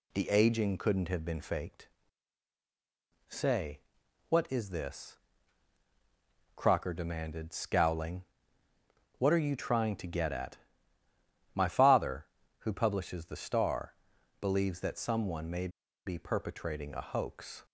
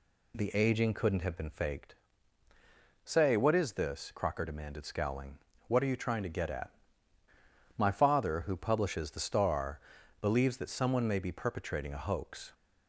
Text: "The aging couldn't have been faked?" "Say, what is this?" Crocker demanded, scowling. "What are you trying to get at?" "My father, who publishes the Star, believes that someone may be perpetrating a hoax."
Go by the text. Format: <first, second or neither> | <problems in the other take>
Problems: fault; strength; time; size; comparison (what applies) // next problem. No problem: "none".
second | pauses between "may" and "be"; at 15.6 s; 0.37 s long